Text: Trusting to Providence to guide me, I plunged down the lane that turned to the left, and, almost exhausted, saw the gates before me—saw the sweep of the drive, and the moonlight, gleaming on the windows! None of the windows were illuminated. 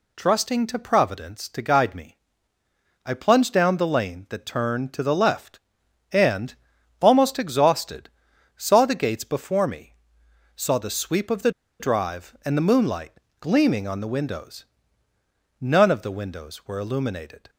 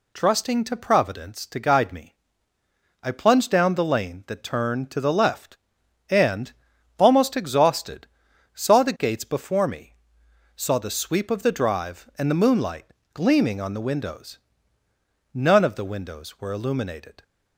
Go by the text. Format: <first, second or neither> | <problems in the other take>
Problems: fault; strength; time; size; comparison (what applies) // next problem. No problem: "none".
second | pauses between "the" and "drive"; slight; at 11.5 s; 0.28 s long